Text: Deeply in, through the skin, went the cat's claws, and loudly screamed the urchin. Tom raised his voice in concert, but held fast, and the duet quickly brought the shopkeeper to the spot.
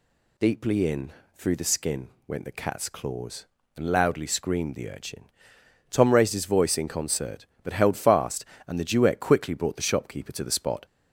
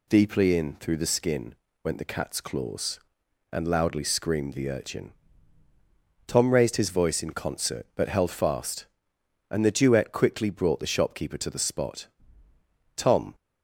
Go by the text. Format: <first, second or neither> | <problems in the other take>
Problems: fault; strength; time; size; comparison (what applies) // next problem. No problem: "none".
first | goes on to say "Tom"; slight; from 12.9 s on; 0.38 s long